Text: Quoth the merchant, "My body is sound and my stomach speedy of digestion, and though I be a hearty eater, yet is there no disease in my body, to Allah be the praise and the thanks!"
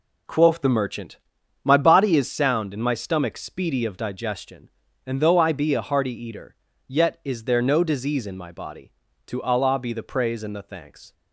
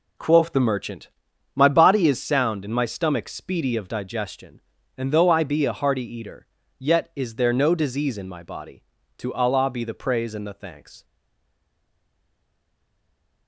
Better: first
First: none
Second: stays silent after the last word; from 11.0 s on; 2.4 s long

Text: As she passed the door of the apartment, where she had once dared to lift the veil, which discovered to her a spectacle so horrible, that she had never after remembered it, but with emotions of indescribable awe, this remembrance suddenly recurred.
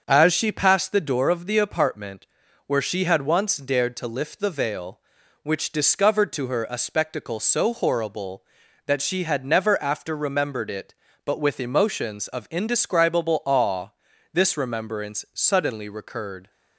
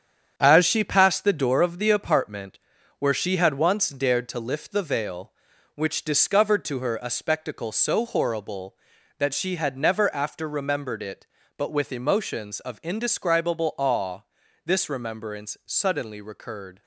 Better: first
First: starts louder than the rest; until 1.0 s; 6.5 dB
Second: gets quieter; throughout; 6.5 dB // starts louder than the rest; strong; until 1.3 s; 8 dB

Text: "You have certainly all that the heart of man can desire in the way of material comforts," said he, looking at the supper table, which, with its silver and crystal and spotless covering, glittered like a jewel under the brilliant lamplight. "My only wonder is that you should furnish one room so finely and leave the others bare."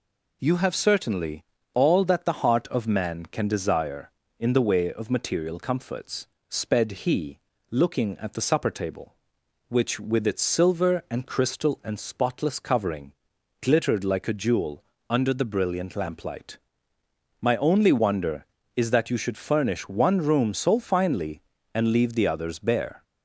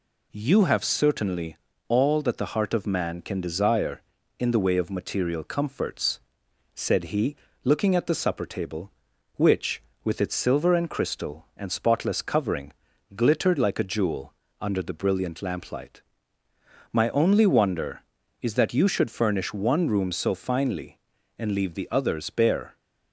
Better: second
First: pauses between "certainly" and "all"; slight; at 1.4 s; 0.30 s long // says "sped" for "said"; at 6.4 s // pauses between "jewel" and "under"; slight; at 14.8 s; 0.28 s long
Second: pauses between "certainly" and "all"; slight; at 1.5 s; 0.30 s long // pauses between "jewel" and "under"; slight; at 14.3 s; 0.26 s long

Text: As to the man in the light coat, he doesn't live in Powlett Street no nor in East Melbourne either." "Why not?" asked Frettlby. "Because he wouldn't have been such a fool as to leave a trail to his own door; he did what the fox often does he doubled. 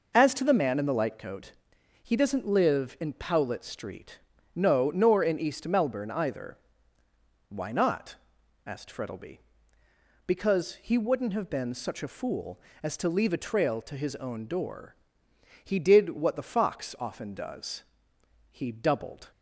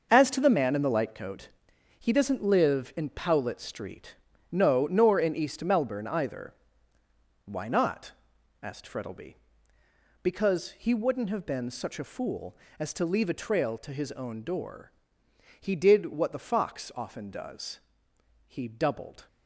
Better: first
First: pauses between "Street" and "no"; slight; at 4.1 s; 0.36 s long // pauses between "does" and "he"; noticeable; at 17.8 s; 0.68 s long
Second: gets quieter; strong; throughout; 9.5 dB // pauses between "Street" and "no"; slight; at 4.1 s; 0.36 s long // pauses between "does" and "he"; noticeable; at 17.7 s; 0.68 s long

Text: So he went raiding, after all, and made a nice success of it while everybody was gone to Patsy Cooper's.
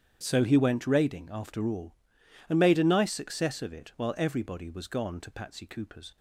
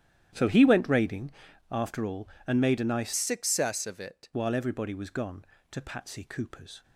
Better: first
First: starts louder than the rest; strong; until 1.2 s; 9 dB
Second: starts louder than the rest; strong; until 1.7 s; 11 dB // changes voice from "success" to "it"; from 3.1 to 4.2 s; 1.1 s long

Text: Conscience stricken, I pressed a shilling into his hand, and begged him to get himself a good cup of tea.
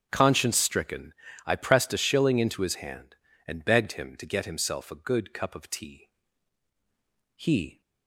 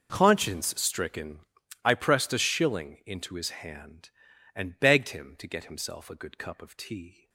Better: second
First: starts louder than the rest; strong; until 1.1 s; 7.5 dB // goes on to say "He"; slight; from 7.3 s on; 0.44 s long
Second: none

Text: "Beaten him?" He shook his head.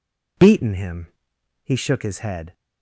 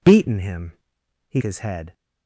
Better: first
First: none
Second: skips "shook"; at 1.4 s

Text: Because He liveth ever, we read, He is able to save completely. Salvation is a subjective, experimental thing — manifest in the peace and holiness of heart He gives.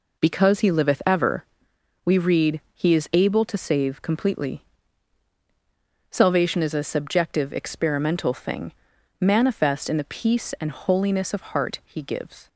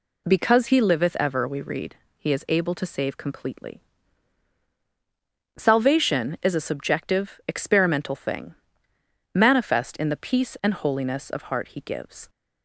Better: neither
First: none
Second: none

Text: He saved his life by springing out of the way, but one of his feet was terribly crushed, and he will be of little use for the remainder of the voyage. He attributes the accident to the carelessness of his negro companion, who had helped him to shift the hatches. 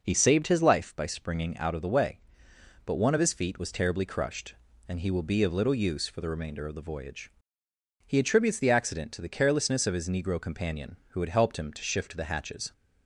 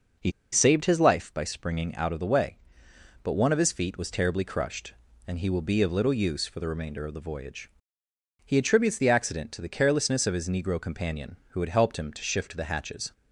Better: first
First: none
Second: pauses between "He" and "saved"; slight; at 0.3 s; 0.20 s long

